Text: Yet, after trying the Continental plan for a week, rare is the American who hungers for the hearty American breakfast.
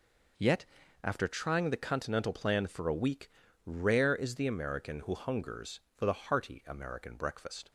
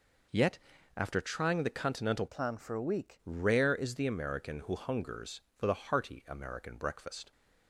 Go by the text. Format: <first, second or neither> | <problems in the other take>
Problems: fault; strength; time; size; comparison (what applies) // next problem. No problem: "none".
first | changes voice from "plan" to "week"; from 2.2 to 3.2 s; 1.0 s long